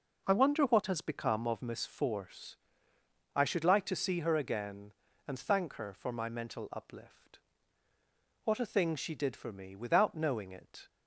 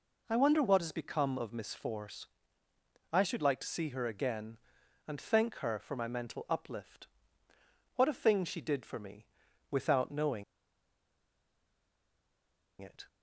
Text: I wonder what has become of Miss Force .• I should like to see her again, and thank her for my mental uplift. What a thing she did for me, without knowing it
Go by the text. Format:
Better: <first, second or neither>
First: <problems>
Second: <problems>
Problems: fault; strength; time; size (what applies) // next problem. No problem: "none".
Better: first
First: none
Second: pauses between "knowing" and "it"; strong; at 10.4 s; 2.3 s long